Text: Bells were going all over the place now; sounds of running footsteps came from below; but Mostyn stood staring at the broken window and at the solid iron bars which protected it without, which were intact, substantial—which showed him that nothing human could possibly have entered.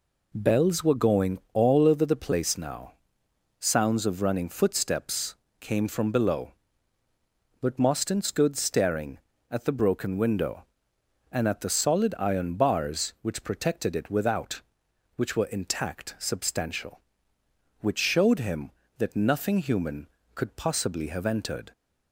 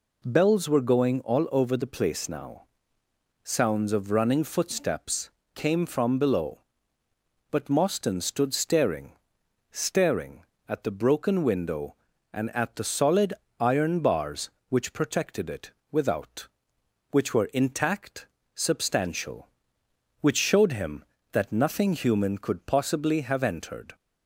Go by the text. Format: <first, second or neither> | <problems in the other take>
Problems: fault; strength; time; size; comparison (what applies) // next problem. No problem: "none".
first | pauses between "footsteps" and "came"; slight; at 5.2 s; 0.24 s long; slight in the first // says "staring" twice; at 9.7 s // pauses between "solid" and "iron"; slight; at 13.3 s; 0.26 s long // pauses between "it" and "without"; slight; at 15.7 s; 0.20 s long